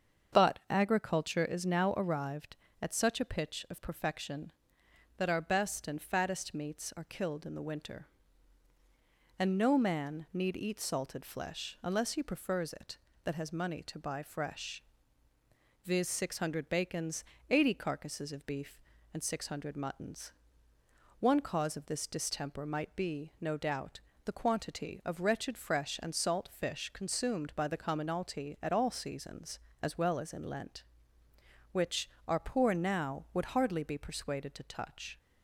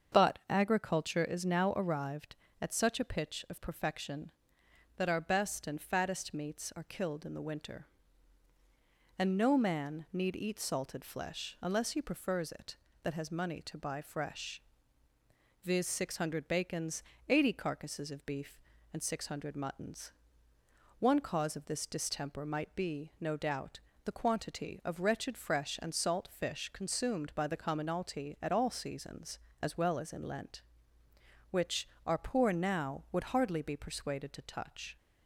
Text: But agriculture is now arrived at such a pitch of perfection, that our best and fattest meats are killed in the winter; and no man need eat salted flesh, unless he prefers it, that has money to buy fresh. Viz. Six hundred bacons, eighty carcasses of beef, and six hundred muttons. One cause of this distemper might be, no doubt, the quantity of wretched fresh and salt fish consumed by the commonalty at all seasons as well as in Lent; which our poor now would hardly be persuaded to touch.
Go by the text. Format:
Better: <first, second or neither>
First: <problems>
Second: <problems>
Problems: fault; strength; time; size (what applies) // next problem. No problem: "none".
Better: neither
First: starts louder than the rest; strong; until 1.4 s; 7 dB // pauses between "which" and "our"; slight; at 32.0 s; 0.16 s long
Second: starts louder than the rest; strong; until 1.2 s; 7 dB // pauses between "which" and "our"; slight; at 31.8 s; 0.16 s long